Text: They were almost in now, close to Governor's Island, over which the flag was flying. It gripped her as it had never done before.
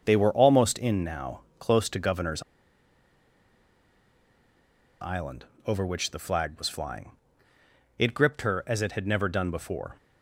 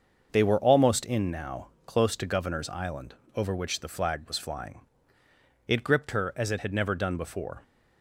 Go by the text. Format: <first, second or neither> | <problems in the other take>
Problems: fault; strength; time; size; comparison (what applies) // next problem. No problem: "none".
second | starts louder than the rest; until 1.0 s; 6.5 dB; also in the second // pauses between "Governor's" and "Island"; strong; at 2.4 s; 2.5 s long